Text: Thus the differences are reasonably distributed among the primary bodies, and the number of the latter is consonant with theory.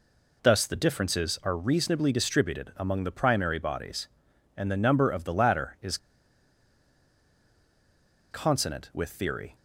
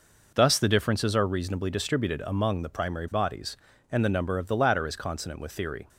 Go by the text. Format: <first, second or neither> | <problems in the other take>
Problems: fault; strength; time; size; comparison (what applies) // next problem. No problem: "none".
second | pauses between "is" and "consonant"; strong; at 5.9 s; 2.3 s long